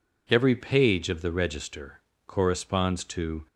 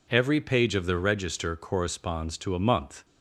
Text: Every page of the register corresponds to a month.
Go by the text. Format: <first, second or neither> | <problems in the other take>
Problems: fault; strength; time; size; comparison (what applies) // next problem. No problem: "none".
second | pauses between "register" and "corresponds"; slight; at 2.0 s; 0.26 s long // stops before "a month"; at 3.4 s